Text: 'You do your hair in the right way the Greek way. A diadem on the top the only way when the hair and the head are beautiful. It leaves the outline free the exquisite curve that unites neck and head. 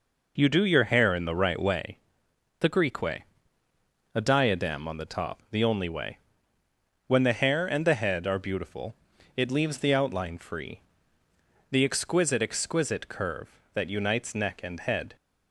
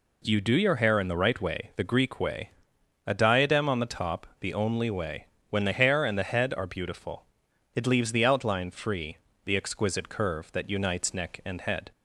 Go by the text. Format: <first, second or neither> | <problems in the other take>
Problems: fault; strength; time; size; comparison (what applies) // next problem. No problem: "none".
second | pauses between "way" and "the"; noticeable; at 1.9 s; 0.62 s long // pauses between "way" and "when"; noticeable; at 6.1 s; 0.88 s long; slight in the second // pauses between "free" and "the"; noticeable; at 10.8 s; 0.90 s long; slight in the second // says "exquisite" twice; at 12.4 s